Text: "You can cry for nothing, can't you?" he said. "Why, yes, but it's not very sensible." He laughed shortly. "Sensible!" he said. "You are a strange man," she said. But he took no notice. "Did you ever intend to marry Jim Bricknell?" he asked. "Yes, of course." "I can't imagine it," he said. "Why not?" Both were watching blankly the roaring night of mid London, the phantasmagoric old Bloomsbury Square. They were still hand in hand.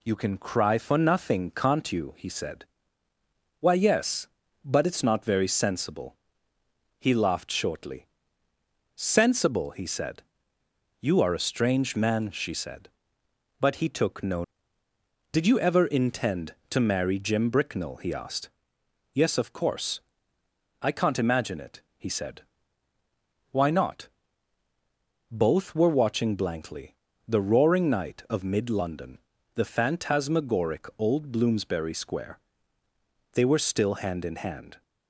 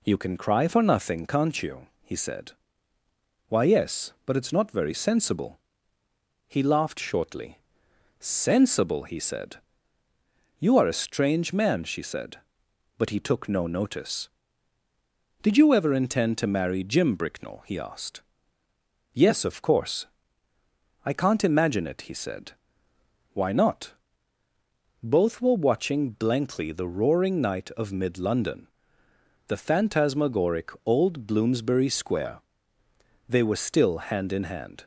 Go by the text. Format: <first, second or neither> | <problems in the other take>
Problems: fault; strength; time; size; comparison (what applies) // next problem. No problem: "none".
second | skips "notice"; at 14.8 s // pauses between "blankly" and "the"; slight; at 26.9 s; 0.32 s long